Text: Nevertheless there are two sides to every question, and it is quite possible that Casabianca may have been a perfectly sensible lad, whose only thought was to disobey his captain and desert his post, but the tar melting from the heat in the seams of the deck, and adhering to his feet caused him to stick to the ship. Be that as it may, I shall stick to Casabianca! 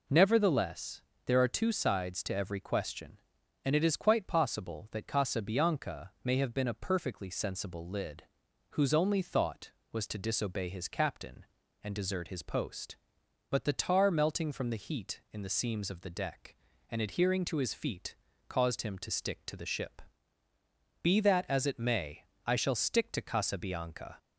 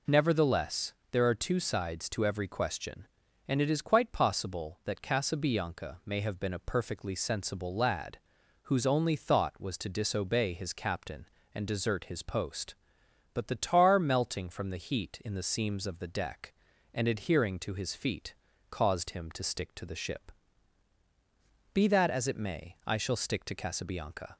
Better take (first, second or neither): second